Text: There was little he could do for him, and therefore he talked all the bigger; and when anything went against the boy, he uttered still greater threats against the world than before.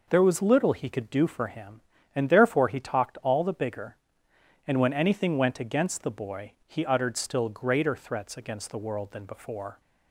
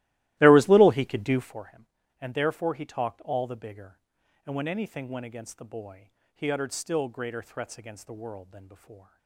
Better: first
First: none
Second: starts louder than the rest; strong; until 1.5 s; 16.5 dB

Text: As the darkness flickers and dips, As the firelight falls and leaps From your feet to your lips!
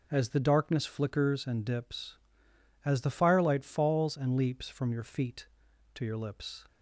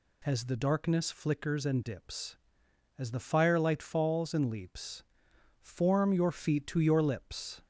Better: first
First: none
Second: says "Form" for "From"; at 5.6 s

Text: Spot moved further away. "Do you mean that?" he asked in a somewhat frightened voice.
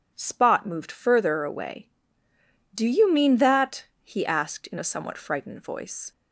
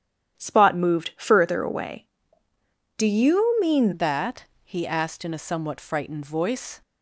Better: first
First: none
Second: starts louder than the rest; strong; until 1.4 s; 10.5 dB // changes voice at "that"; from 3.9 s on; 2.9 s long

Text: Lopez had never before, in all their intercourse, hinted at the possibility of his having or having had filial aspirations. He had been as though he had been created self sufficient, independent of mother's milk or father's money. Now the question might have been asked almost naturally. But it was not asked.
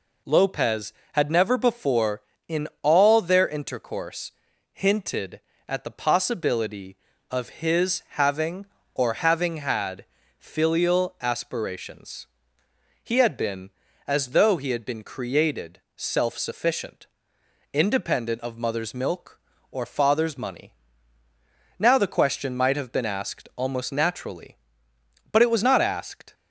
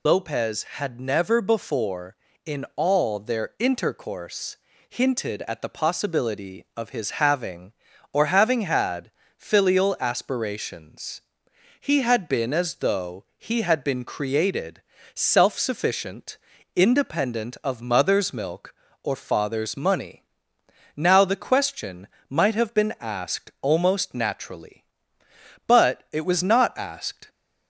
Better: first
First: pauses between "had" and "filial"; slight; at 10.0 s; 0.32 s long // pauses between "created" and "self"; slight; at 15.7 s; 0.16 s long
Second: loses the start of "Lopez"; at 0.0 s; 100 ms // pauses between "had" and "filial"; slight; at 9.1 s; 0.26 s long // pauses between "created" and "self"; slight; at 14.8 s; 0.34 s long // pauses between "question" and "might"; slight; at 22.0 s; 0.22 s long

